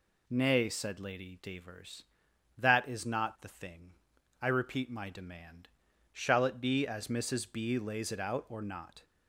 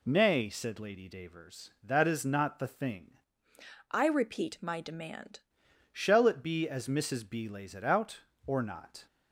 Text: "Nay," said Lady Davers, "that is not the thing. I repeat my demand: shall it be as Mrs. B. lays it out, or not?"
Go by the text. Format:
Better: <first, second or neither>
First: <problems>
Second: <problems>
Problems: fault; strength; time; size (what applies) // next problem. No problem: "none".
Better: first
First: none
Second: changes voice from "I" to "demand"; from 3.9 to 5.4 s; 1.5 s long